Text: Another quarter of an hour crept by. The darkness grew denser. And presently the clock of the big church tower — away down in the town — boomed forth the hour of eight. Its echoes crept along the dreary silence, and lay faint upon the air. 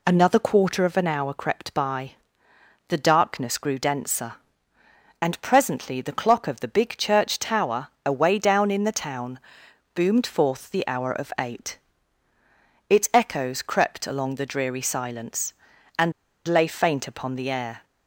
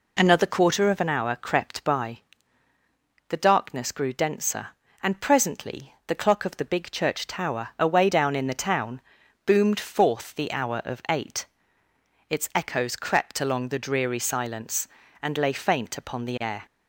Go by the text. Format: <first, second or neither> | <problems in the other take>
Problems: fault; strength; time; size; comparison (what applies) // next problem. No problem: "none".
second | pauses between "and" and "lay"; slight; at 16.1 s; 0.36 s long